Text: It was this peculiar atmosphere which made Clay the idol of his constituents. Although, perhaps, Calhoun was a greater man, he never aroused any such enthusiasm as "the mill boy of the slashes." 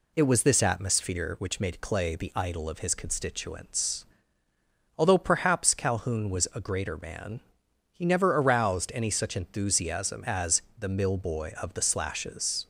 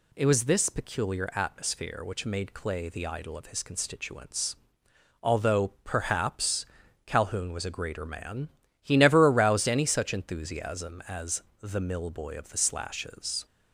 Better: second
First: skips "peculiar"; at 0.6 s // pauses between "as" and "the"; slight; at 10.6 s; 0.18 s long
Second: pauses between "as" and "the"; slight; at 11.4 s; 0.20 s long

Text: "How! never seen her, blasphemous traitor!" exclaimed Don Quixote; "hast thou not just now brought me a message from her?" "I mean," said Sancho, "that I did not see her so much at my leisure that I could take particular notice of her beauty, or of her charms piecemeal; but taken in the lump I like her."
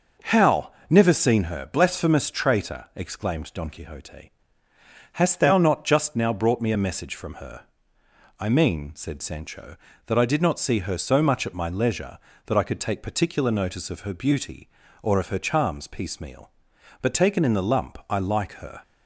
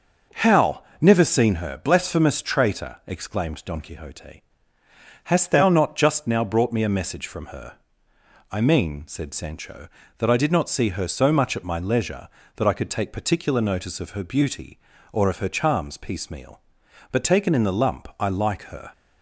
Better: neither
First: none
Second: none

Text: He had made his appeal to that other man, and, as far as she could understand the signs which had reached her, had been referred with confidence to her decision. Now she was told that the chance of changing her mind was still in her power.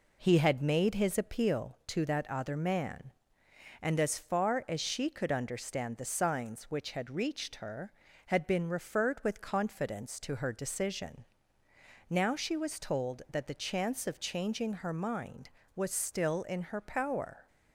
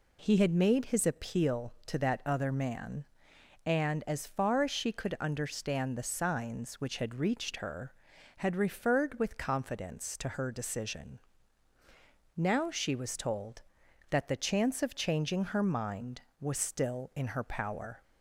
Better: first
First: none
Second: skips "been"; at 8.5 s

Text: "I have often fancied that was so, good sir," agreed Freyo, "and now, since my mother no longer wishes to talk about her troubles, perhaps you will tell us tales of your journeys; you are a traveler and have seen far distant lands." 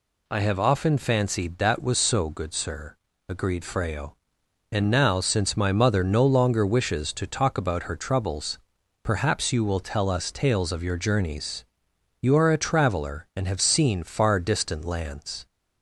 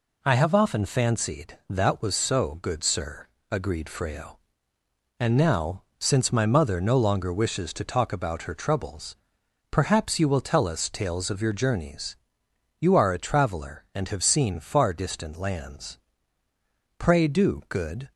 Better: first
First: none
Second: goes on to say "Pray do good"; noticeable; from 16.9 s on; 1.1 s long

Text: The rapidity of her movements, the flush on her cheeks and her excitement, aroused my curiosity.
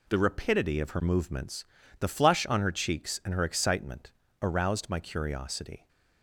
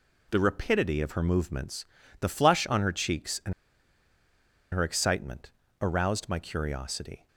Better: first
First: none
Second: pauses between "and" and "her"; at 3.5 s; 1.2 s long

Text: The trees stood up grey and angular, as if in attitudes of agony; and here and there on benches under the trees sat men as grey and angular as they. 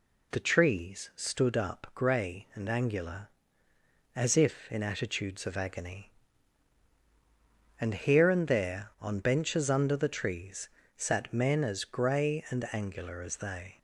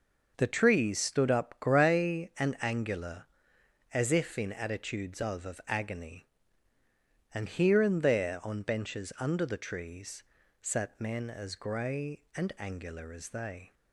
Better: first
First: pauses between "trees" and "sat"; slight; at 10.6 s; 0.26 s long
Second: says "of" twice; at 5.4 s // pauses between "trees" and "sat"; slight; at 10.2 s; 0.36 s long

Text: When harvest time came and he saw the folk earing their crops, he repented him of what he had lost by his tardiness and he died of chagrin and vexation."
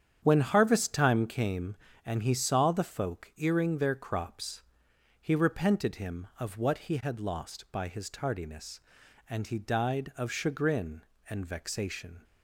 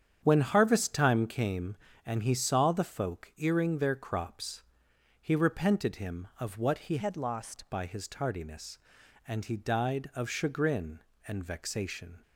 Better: first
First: starts louder than the rest; strong; until 1.2 s; 8.5 dB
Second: starts louder than the rest; strong; until 1.2 s; 8.5 dB // changes voice from "had" to "lost"; from 6.9 to 7.6 s; 0.7 s long

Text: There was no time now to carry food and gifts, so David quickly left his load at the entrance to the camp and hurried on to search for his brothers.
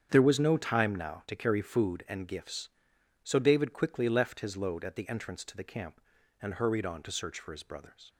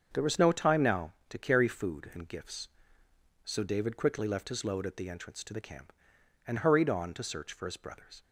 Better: neither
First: starts louder than the rest; strong; until 1.1 s; 8 dB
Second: starts louder than the rest; until 1.1 s; 7 dB

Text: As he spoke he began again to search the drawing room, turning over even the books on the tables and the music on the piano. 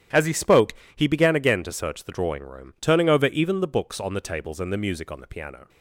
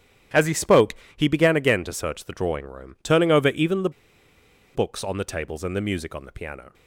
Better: first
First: starts louder than the rest; strong; until 1.3 s; 10.5 dB // pauses between "spoke" and "he"; slight; at 0.7 s; 0.22 s long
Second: starts louder than the rest; strong; until 1.5 s; 10.5 dB // pauses between "spoke" and "he"; slight; at 0.9 s; 0.22 s long // pauses between "the" and "books"; noticeable; at 3.8 s; 0.84 s long

